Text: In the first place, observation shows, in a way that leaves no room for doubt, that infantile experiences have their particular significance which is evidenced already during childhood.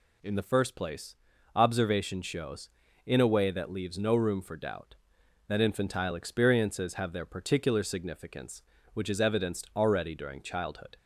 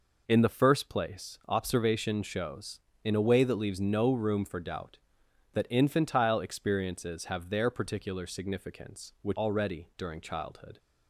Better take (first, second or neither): first